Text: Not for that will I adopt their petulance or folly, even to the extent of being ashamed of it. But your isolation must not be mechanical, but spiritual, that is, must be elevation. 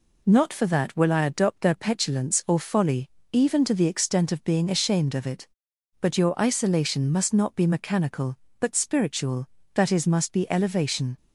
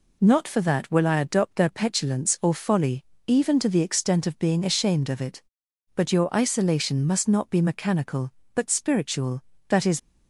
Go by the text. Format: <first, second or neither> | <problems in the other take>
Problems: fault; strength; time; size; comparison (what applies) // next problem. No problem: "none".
first | stops before "must be elevation"; at 9.9 s